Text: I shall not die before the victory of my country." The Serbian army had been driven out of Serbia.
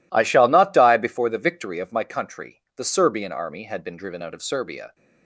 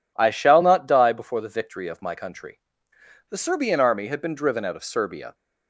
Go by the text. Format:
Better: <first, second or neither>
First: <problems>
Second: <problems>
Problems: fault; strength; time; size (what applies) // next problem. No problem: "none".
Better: neither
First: none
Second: none